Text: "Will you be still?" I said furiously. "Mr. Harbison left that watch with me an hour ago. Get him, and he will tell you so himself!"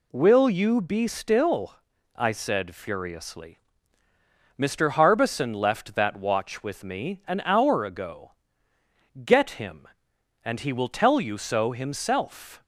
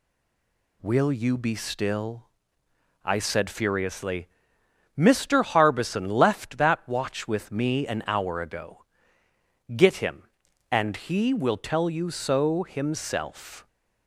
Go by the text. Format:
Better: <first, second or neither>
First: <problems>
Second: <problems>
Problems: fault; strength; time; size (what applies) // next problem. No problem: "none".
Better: first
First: none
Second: stays silent before the first word; slight; until 0.8 s; 0.8 s long